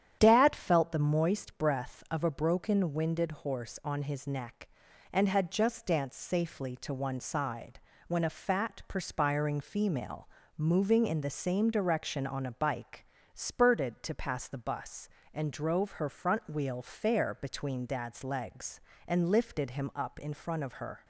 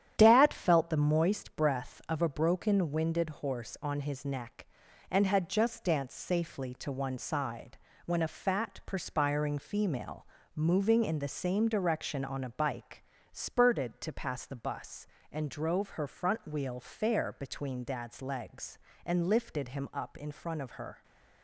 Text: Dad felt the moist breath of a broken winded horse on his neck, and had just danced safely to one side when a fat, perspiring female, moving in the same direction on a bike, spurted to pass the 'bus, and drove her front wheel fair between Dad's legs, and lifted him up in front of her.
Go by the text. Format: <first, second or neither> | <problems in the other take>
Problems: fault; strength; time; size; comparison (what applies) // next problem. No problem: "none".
first | gets quieter; noticeable; throughout; 6 dB // starts louder than the rest; strong; until 1.1 s; 10.5 dB; strong in the first // pauses between "side" and "when"; slight; at 7.7 s; 0.26 s long; slight in the first